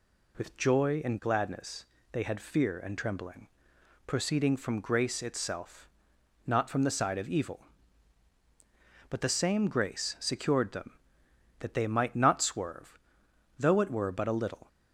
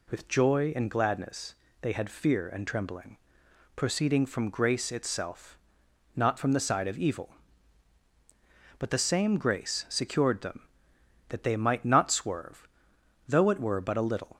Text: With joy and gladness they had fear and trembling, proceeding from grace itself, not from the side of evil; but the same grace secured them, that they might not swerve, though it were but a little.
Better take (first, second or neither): neither